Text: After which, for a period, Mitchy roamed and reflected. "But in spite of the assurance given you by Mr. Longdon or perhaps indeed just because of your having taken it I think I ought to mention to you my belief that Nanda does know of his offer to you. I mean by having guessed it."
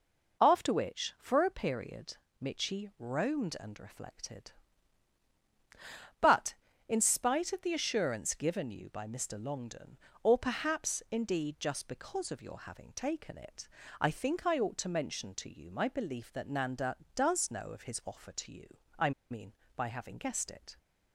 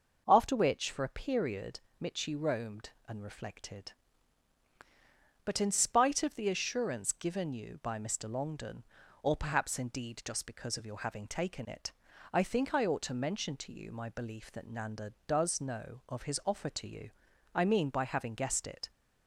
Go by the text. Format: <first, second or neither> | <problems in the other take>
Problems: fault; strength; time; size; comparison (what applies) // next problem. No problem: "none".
second | pauses between "it" and "I"; slight; at 13.6 s; 0.34 s long; also in the second // pauses between "I" and "mean"; slight; at 19.1 s; 0.20 s long